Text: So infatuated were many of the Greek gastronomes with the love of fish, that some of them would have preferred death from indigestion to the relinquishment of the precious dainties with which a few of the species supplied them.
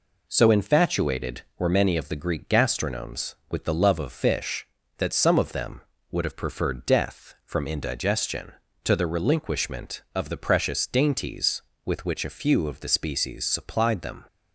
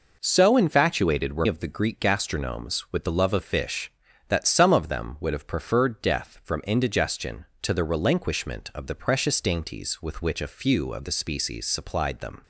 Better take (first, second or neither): first